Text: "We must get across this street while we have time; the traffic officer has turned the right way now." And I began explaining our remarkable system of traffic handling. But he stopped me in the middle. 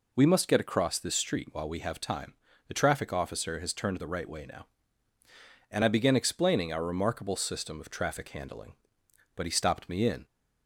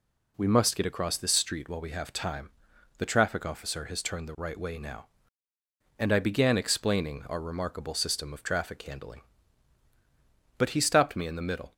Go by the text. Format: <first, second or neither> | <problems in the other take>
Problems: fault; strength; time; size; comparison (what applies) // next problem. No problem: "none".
second | stops before "the middle"; at 10.2 s